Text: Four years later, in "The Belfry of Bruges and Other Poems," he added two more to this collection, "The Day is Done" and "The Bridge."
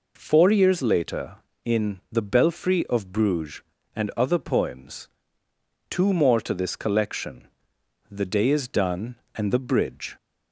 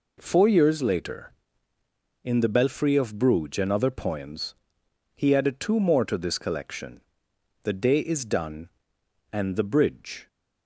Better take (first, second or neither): second